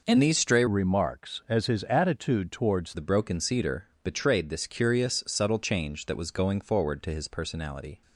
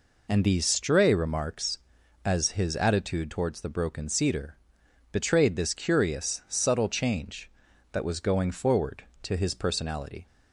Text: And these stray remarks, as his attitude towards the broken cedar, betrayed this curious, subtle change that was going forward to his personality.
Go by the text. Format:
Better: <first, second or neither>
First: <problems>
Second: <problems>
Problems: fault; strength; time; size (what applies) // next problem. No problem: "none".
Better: second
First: changes voice from "remarks" to "towards"; from 0.6 to 2.9 s; 2.3 s long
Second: none